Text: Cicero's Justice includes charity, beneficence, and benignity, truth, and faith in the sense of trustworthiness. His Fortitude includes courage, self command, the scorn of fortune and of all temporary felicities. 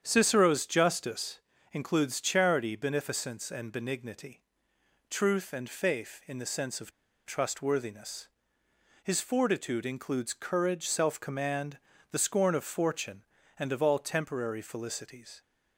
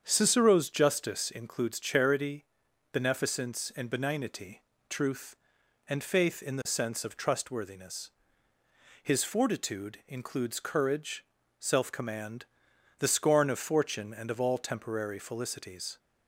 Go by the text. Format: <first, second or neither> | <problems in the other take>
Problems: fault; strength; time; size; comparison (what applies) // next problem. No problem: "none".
second | starts louder than the rest; strong; until 1.0 s; 8.5 dB; strong in the second // pauses between "Justice" and "includes"; slight; at 1.3 s; 0.32 s long // pauses between "of" and "trustworthiness"; at 6.9 s; 0.36 s long